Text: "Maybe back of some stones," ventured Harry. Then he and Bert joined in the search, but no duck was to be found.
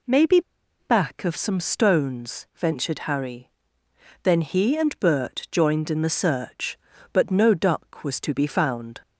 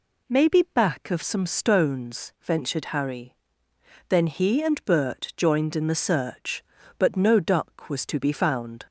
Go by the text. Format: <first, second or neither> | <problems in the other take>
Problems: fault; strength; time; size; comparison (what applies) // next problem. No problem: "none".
second | pauses between "Maybe" and "back"; at 0.4 s; 0.39 s long